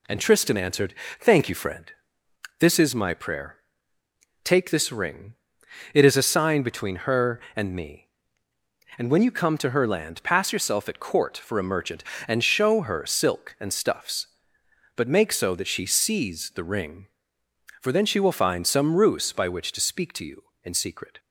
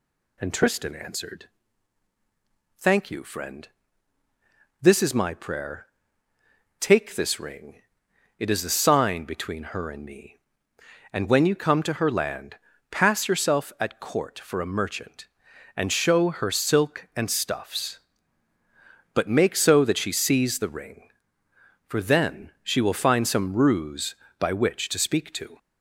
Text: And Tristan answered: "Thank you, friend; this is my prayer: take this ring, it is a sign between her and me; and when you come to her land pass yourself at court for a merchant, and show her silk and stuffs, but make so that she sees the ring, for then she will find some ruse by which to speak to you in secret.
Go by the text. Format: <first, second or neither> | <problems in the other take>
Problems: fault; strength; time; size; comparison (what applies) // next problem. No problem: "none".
first | pauses between "land" and "pass"; slight; at 12.5 s; 0.34 s long // stops before "you in secret"; at 25.5 s